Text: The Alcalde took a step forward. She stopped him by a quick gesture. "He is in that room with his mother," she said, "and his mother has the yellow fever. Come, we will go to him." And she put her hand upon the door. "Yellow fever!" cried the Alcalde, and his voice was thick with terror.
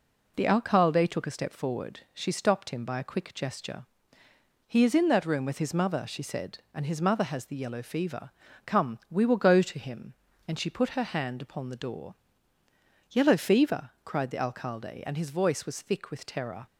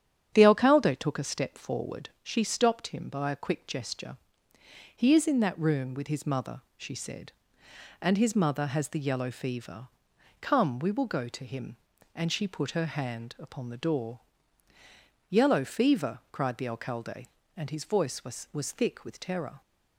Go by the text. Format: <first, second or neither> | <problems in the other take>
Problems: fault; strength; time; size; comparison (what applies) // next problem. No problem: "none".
first | starts louder than the rest; strong; until 1.3 s; 9 dB // says "was" twice; at 18.5 s